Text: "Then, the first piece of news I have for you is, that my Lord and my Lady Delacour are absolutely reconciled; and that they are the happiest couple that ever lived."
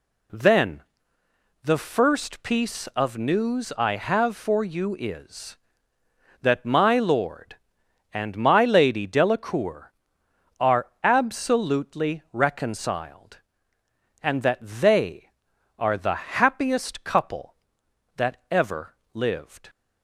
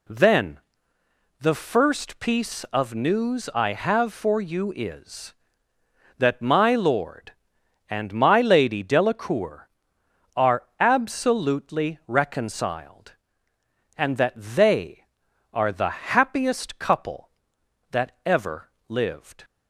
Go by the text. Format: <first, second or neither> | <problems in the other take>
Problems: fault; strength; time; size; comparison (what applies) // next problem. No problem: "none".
neither | pauses between "ever" and "lived"; slight; the same in both